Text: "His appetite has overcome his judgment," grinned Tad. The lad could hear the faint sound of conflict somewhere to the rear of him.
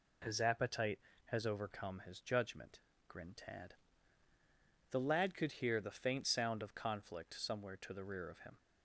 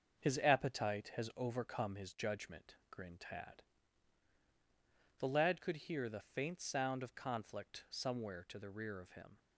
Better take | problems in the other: first | gets quieter; noticeable; throughout; 5 dB

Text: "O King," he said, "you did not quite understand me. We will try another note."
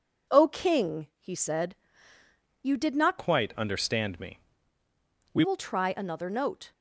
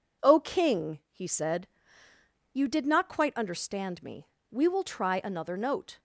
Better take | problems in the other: second | changes voice from "quite" to "We"; from 3.1 to 5.4 s; 2.3 s long

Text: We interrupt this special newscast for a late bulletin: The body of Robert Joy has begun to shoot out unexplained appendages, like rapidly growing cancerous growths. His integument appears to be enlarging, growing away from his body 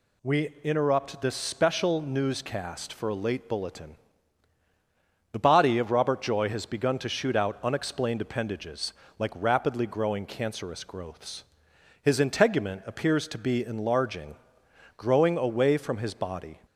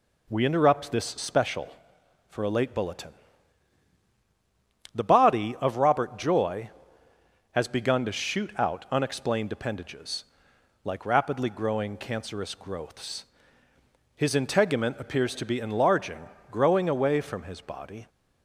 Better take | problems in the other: first | skips "newscast"; at 2.0 s

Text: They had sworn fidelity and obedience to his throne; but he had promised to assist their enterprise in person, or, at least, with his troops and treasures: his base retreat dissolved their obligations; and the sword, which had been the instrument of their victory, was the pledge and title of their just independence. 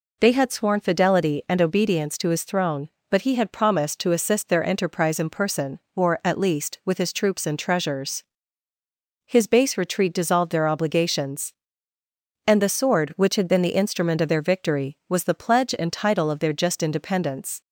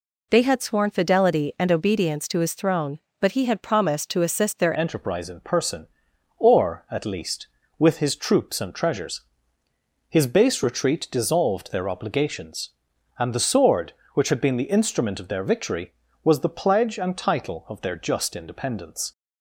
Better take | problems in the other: first | changes voice at "enterprise"; from 4.7 s on; 14.4 s long

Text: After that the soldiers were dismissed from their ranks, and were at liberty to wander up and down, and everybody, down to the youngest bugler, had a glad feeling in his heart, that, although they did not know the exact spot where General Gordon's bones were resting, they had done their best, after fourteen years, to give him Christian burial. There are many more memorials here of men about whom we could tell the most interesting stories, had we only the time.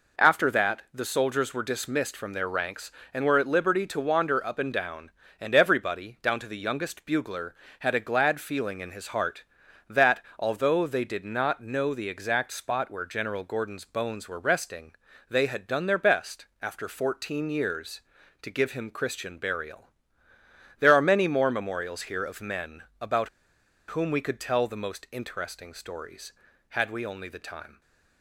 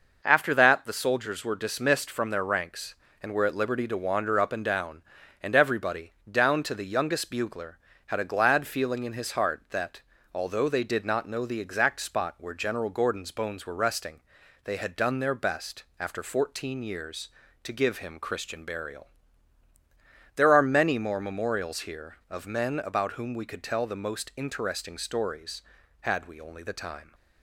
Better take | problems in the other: second | pauses between "men" and "about"; slight; at 22.8 s; 0.18 s long // pauses between "about" and "whom"; noticeable; at 23.2 s; 0.59 s long

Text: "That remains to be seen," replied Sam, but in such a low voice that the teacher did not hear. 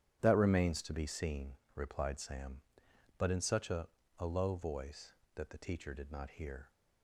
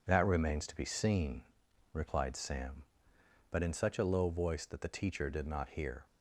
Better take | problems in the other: second | starts louder than the rest; strong; until 1.2 s; 10 dB // says "a" twice; at 4.1 s

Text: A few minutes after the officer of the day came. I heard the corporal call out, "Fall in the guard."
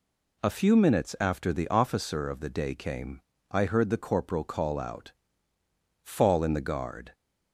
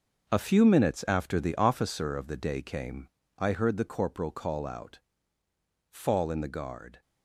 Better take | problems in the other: first | gets quieter; strong; throughout; 10 dB

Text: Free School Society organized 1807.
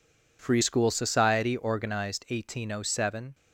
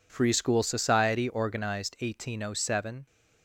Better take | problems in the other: neither | none

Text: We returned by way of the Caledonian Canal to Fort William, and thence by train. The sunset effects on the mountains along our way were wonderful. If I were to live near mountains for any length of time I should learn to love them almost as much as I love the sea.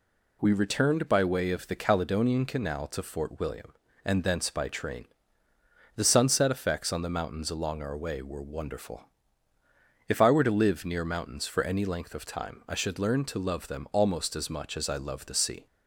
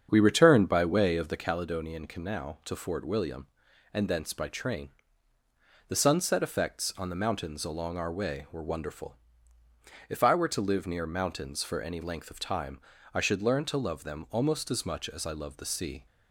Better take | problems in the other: first | starts louder than the rest; strong; until 1.5 s; 7.5 dB // pauses between "time" and "I"; slight; at 12.7 s; 0.34 s long

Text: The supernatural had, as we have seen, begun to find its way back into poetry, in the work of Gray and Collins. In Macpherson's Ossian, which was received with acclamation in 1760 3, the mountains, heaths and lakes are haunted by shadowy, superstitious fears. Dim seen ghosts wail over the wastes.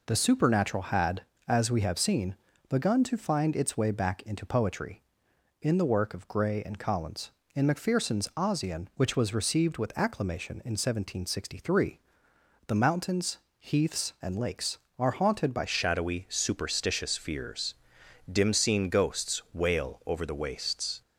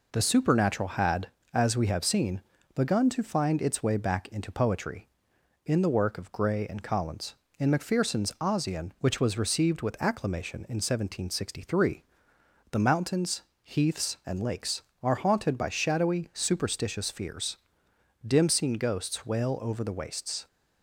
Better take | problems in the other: second | changes voice at "shadowy"; from 15.6 s on; 5.4 s long

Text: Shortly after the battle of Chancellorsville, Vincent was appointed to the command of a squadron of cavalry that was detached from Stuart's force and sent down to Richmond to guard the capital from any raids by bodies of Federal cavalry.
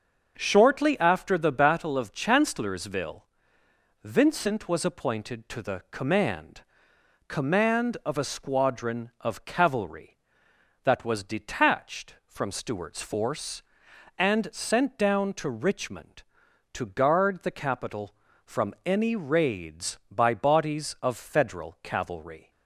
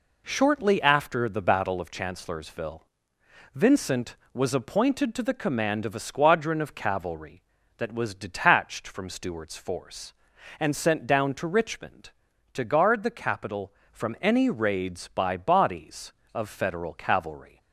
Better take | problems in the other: second | starts louder than the rest; until 1.3 s; 6.5 dB // says "command" twice; at 7.2 s

